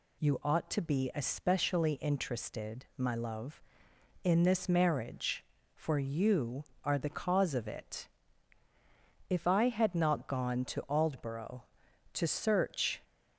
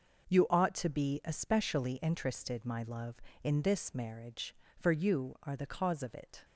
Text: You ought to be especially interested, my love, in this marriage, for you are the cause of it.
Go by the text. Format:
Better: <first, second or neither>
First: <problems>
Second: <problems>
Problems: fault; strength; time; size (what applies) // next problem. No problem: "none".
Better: second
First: goes on to say "If I had not gone to Aldborough to search"; strong; from 9.2 s on; 3.7 s long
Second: none